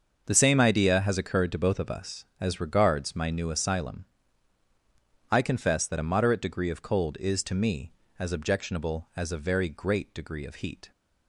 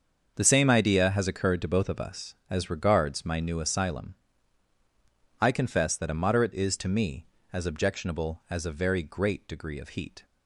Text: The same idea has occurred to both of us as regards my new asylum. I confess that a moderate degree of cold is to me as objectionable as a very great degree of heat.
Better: first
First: starts louder than the rest; until 1.2 s; 6.5 dB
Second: starts louder than the rest; until 1.3 s; 6.5 dB // skips "degree of cold"; at 6.5 s

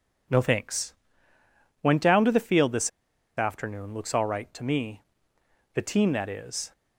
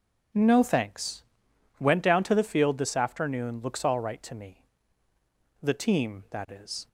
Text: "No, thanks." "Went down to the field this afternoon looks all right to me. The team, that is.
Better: second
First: pauses between "this" and "afternoon"; noticeable; at 2.8 s; 0.48 s long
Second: none

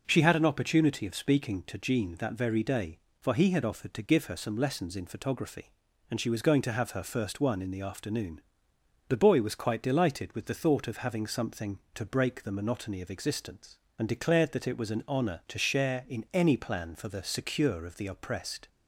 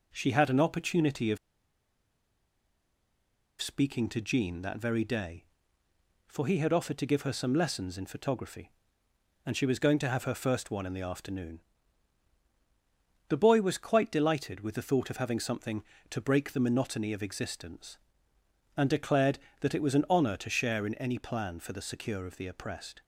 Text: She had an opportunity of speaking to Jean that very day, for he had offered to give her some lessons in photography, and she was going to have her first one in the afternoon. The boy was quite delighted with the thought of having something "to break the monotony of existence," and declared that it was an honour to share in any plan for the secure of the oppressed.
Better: first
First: none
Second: pauses between "of" and "speaking"; strong; at 1.3 s; 2.2 s long

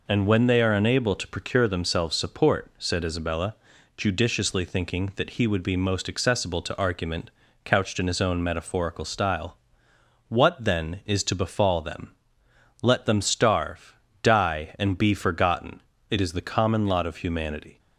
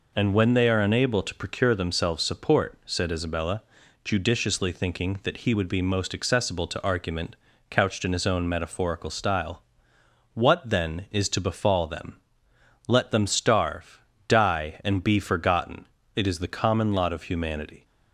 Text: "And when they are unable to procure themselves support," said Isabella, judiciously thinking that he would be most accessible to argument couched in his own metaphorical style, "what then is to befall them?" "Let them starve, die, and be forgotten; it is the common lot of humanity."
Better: neither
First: pauses between "argument" and "couched"; slight; at 7.2 s; 0.34 s long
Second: pauses between "argument" and "couched"; slight; at 7.3 s; 0.34 s long

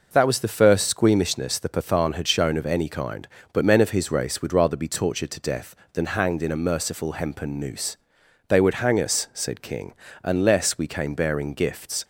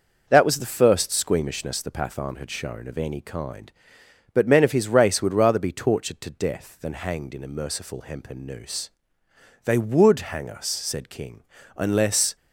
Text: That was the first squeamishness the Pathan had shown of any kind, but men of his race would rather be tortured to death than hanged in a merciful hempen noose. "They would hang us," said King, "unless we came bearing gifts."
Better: first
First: none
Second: stops before "we came bearing gifts"; at 12.3 s

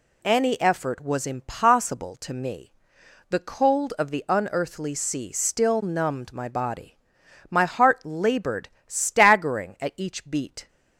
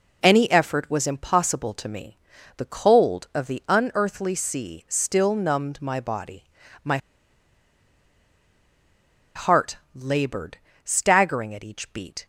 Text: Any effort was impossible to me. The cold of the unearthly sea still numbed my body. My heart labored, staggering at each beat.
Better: first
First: none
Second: pauses between "My" and "heart"; strong; at 6.9 s; 2.3 s long // pauses between "heart" and "labored"; slight; at 9.7 s; 0.18 s long

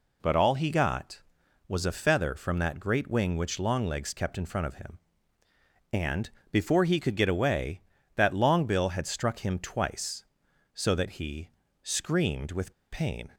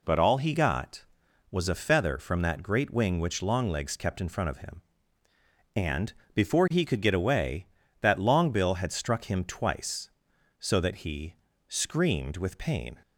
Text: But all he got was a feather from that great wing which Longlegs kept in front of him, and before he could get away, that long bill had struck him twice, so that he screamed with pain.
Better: second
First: pauses between "and" and "before"; slight; at 6.2 s; 0.22 s long // pauses between "he" and "screamed"; slight; at 11.4 s; 0.32 s long // pauses between "with" and "pain"; slight; at 12.7 s; 0.18 s long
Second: pauses between "and" and "before"; slight; at 6.1 s; 0.22 s long // pauses between "he" and "screamed"; slight; at 11.3 s; 0.32 s long

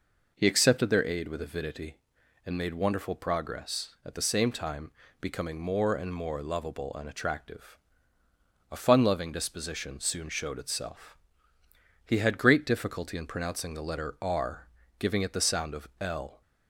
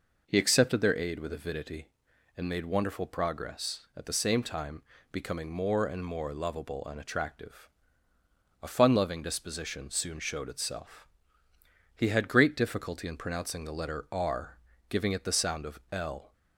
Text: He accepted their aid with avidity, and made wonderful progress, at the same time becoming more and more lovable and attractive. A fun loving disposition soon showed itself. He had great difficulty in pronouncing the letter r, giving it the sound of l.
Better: neither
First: pauses between "time" and "becoming"; slight; at 4.9 s; 0.30 s long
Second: pauses between "time" and "becoming"; slight; at 4.8 s; 0.30 s long

